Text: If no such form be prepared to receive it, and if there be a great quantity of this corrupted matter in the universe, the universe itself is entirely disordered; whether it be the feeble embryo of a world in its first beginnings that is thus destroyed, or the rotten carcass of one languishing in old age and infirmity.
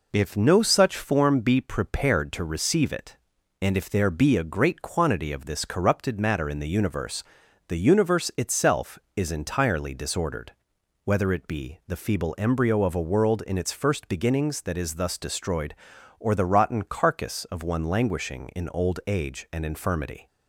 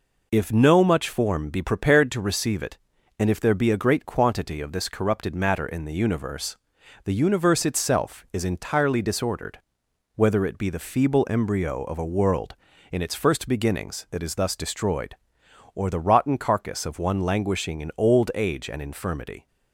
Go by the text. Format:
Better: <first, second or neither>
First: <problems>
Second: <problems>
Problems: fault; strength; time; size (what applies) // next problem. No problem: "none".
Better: first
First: none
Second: says "much" for "such"; at 0.8 s